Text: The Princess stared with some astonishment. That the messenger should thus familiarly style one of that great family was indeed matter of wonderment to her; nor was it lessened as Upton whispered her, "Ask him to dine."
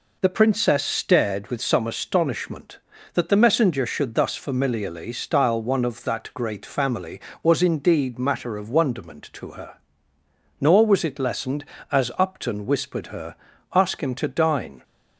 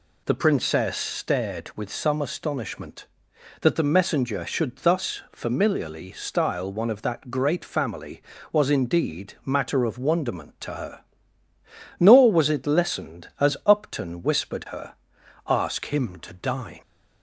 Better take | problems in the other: neither | none

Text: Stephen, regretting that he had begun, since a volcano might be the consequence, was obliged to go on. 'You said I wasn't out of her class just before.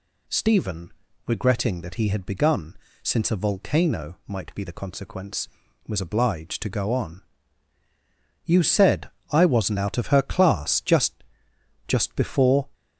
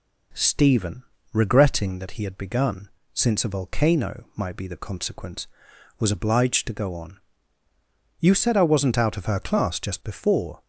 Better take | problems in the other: second | pauses between "said" and "I"; slight; at 9.0 s; 0.22 s long // says "just" twice; at 11.8 s

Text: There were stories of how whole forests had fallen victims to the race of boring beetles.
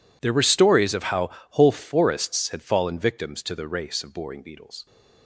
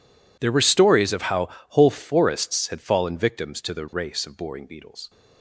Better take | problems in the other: neither | pauses between "how" and "whole"; slight; the same in both

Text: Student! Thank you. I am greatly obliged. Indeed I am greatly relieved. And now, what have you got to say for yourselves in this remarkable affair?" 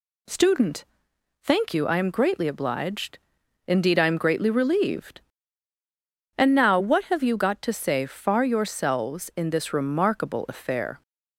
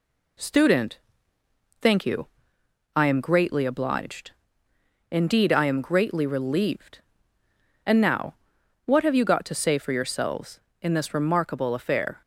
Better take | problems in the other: second | says "far" for "for"; at 8.0 s

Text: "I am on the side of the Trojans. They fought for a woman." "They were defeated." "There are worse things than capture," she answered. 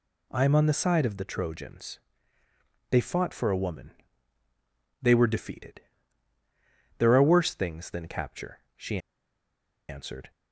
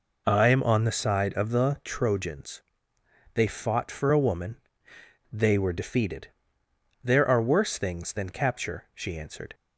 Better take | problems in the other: second | pauses between "she" and "answered"; noticeable; at 8.9 s; 0.90 s long

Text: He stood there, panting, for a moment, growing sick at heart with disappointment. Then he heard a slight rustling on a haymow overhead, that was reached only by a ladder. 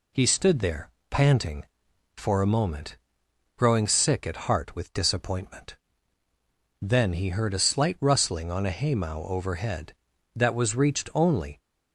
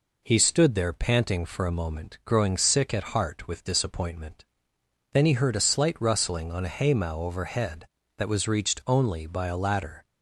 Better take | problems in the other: second | stops before "by a ladder"; at 11.5 s

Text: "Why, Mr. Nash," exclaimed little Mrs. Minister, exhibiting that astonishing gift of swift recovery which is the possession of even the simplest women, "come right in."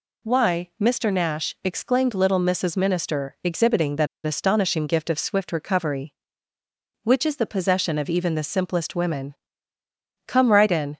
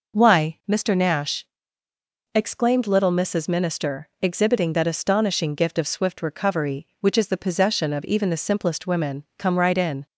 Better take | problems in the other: second | pauses between "that" and "astonishing"; slight; at 4.0 s; 0.18 s long

